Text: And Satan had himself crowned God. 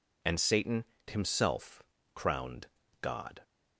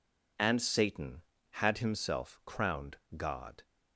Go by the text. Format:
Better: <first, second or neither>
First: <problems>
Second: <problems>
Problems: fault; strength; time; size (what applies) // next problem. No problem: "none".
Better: second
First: skips "had"; at 0.9 s // pauses between "himself" and "crowned"; slight; at 1.8 s; 0.32 s long // pauses between "crowned" and "God"; slight; at 2.6 s; 0.34 s long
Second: pauses between "crowned" and "God"; slight; at 2.9 s; 0.18 s long